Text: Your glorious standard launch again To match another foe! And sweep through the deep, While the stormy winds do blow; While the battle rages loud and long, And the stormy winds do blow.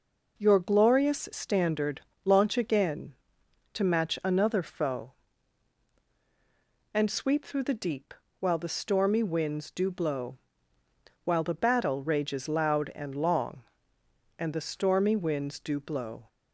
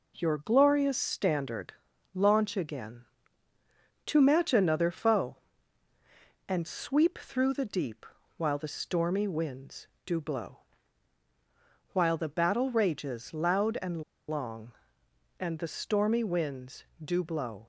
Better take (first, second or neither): first